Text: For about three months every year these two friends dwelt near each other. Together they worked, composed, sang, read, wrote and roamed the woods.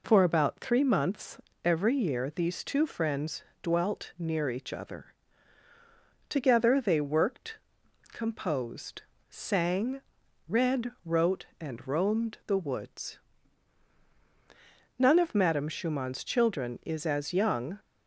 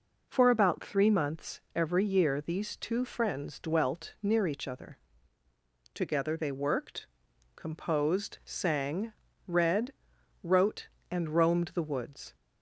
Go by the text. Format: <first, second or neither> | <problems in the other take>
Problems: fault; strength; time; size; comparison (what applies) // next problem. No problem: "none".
second | pauses between "months" and "every"; slight; at 1.3 s; 0.24 s long; slight in the second // pauses between "friends" and "dwelt"; slight; at 3.4 s; 0.22 s long // goes on to say "None of Madame Schumann's children is as young"; strong; from 14.9 s on; 2.8 s long